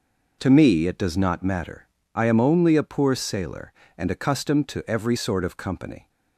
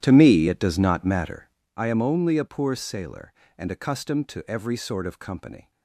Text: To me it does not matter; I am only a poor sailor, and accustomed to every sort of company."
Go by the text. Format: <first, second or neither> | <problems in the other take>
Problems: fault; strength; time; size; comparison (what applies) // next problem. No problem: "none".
first | starts louder than the rest; strong; until 1.7 s; 11.5 dB